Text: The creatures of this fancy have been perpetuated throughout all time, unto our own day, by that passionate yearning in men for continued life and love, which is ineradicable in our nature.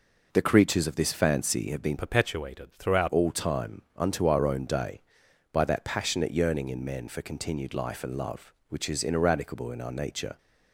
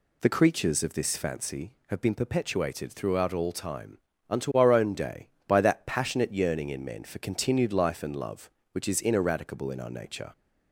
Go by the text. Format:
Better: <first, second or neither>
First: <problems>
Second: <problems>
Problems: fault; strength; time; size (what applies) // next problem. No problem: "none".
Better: second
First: changes voice from "perpetuated" to "throughout"; from 1.9 to 3.0 s; 1.1 s long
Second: none